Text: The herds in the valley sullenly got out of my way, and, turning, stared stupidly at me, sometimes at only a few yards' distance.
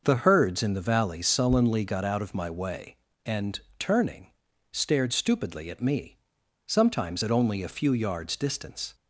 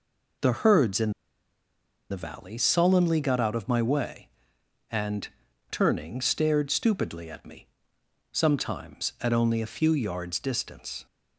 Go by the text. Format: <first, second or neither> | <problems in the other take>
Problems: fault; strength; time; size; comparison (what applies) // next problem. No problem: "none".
first | pauses between "in" and "the"; at 1.1 s; 1.0 s long